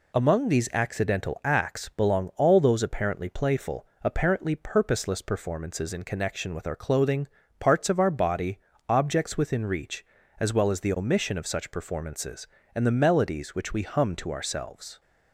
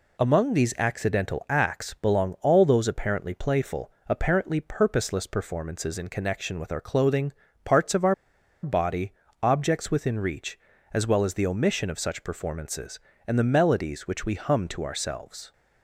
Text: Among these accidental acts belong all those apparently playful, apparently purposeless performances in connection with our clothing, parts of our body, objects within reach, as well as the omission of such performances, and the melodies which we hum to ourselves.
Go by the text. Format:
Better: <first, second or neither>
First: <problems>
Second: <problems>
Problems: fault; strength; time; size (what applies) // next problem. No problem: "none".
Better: first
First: none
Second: pauses between "our" and "body"; noticeable; at 8.1 s; 0.49 s long